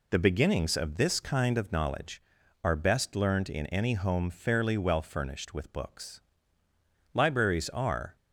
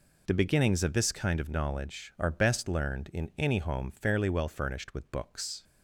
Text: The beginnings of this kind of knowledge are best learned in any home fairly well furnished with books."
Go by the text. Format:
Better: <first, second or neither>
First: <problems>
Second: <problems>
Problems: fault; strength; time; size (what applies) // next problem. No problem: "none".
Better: second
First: goes on to say "Libraries are"; noticeable; from 7.1 s on; 1.0 s long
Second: none